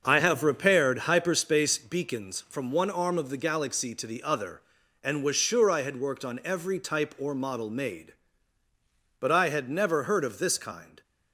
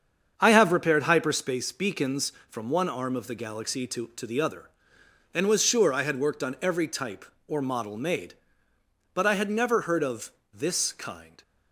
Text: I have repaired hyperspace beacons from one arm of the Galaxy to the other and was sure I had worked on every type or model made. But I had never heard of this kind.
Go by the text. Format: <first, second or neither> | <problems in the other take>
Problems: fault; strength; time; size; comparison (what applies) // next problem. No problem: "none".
first | starts louder than the rest; strong; until 1.3 s; 7.5 dB; also in the first // says "to" twice; at 4.1 s // pauses between "of" and "this"; slight; at 10.3 s; 0.22 s long